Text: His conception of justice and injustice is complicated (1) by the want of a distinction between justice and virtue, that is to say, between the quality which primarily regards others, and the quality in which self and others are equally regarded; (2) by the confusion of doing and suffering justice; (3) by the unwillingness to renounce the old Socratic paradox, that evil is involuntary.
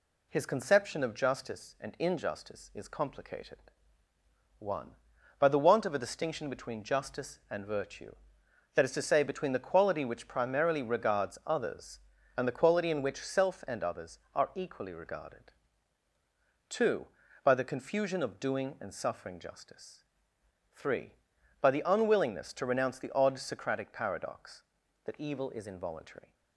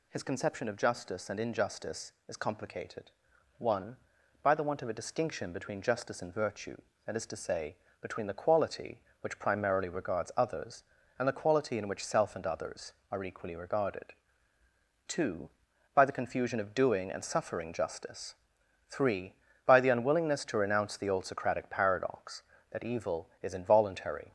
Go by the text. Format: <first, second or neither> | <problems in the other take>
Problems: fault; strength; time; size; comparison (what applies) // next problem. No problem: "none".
second | says "odd" for "old"; at 23.1 s